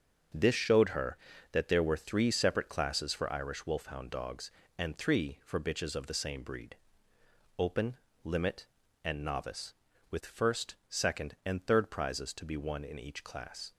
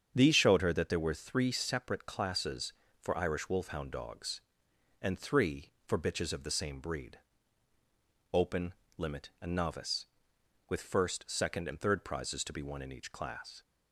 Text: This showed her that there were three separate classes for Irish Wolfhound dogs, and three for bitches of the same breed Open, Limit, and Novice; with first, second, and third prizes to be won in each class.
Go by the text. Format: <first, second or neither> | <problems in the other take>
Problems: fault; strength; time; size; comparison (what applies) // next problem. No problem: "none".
first | starts louder than the rest; strong; until 1.1 s; 8 dB; also in the first // says "These" for "This"; at 0.1 s // pauses between "breed" and "Open"; at 7.1 s; 1.1 s long; noticeable in the first